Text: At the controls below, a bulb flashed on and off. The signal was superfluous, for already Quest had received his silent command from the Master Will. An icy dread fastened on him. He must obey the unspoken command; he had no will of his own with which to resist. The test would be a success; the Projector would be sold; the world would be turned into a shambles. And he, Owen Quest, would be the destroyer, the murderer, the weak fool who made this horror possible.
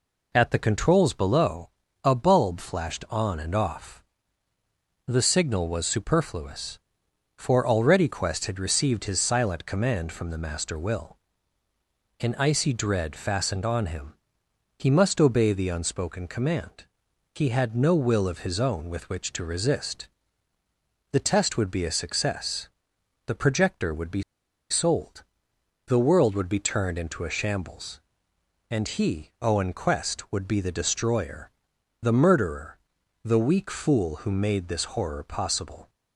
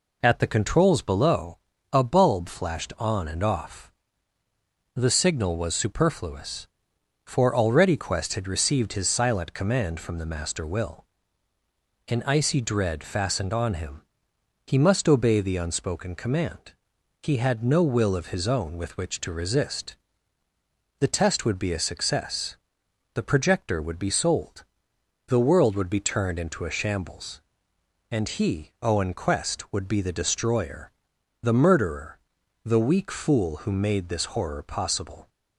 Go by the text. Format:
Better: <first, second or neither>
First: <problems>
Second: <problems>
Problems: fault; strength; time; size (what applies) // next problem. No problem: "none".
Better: second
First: pauses between "be" and "sold"; noticeable; at 24.2 s; 0.48 s long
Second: none